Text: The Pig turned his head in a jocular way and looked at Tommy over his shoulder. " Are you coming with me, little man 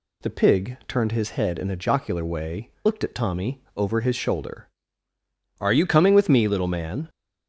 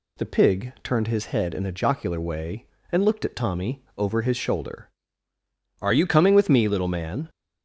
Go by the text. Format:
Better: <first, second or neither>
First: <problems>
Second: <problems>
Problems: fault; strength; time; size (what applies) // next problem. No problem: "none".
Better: second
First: skips "and"; at 2.7 s // pauses between "Tommy" and "over"; slight; at 3.6 s; 0.16 s long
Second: pauses between "Tommy" and "over"; slight; at 3.8 s; 0.16 s long